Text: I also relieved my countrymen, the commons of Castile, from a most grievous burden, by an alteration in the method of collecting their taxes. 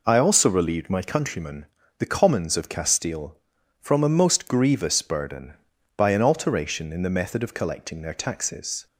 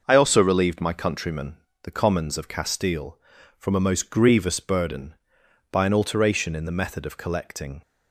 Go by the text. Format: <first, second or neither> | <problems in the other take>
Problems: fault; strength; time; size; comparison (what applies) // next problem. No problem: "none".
first | stops before "their taxes"; at 7.8 s